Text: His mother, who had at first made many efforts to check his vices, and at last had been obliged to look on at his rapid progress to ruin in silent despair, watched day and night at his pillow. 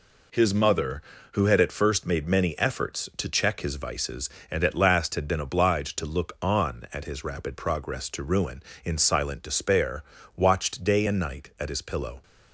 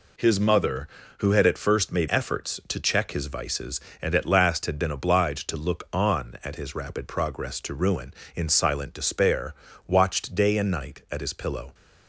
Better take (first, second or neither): first